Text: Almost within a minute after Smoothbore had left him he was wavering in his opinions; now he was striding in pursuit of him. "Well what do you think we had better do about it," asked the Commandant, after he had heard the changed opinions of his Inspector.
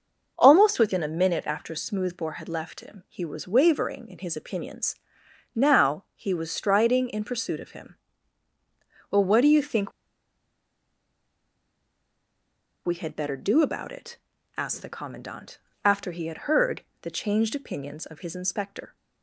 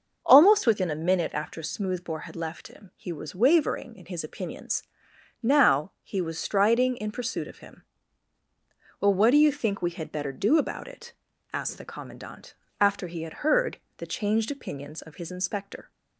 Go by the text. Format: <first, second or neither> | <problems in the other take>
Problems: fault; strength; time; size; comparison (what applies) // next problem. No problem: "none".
second | starts louder than the rest; noticeable; until 1.3 s; 6 dB; noticeable in the second // pauses between "think" and "we"; strong; at 9.9 s; 2.9 s long // pauses between "heard" and "the"; slight; at 16.8 s; 0.20 s long; slight in the second